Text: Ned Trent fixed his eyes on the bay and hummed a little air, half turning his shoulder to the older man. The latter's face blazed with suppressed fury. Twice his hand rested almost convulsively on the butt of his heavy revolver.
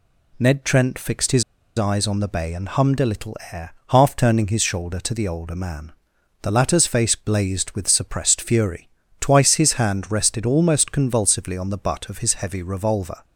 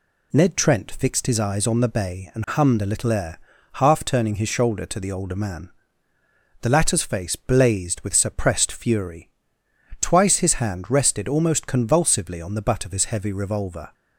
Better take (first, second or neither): second